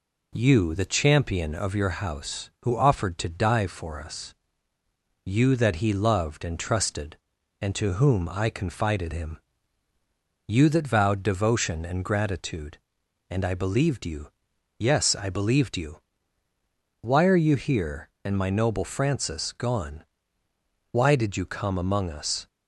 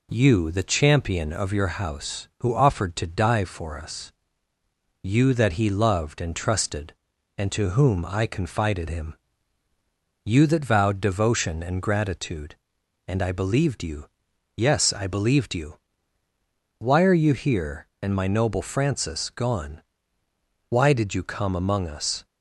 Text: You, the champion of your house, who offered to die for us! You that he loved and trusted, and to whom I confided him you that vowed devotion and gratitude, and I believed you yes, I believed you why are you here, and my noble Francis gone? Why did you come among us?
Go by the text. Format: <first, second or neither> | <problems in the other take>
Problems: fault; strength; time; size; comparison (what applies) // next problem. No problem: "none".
neither | pauses between "him" and "you"; the same in both // pauses between "you" and "yes"; noticeable; the same in both // pauses between "you" and "why"; the same in both